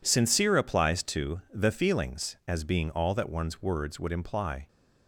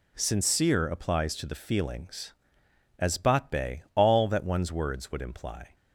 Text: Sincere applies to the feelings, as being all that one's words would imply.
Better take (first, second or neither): first